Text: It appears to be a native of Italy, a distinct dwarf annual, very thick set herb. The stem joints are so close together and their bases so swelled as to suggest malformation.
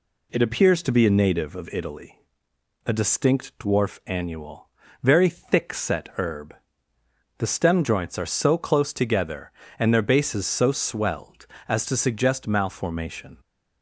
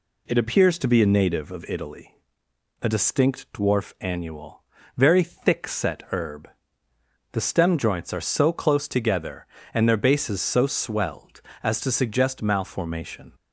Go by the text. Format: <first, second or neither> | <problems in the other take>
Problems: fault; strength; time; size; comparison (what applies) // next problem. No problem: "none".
neither | none